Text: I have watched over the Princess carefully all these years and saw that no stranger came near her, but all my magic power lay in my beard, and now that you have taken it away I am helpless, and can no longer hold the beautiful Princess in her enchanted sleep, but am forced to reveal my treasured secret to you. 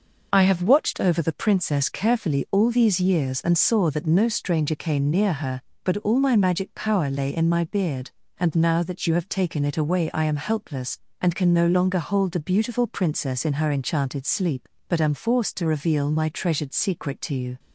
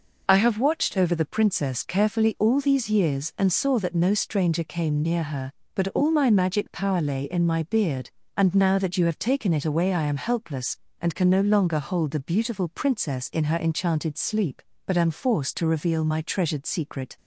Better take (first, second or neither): first